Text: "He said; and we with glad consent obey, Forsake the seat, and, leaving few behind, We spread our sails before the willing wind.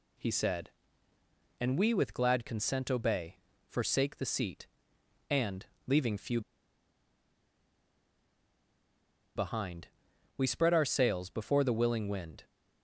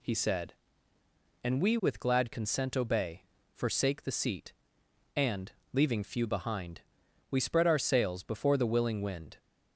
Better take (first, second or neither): second